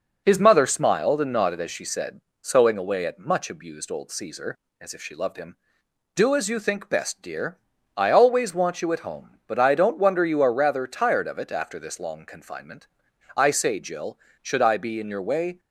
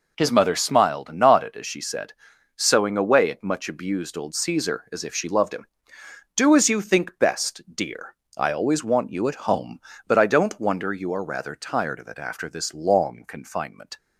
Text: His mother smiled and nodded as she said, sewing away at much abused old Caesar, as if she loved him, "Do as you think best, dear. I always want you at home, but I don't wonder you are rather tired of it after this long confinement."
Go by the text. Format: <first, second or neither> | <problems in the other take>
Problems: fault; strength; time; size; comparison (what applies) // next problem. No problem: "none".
second | goes on to say "I say Jill should I be in your way"; strong; from 13.3 s on; 2.2 s long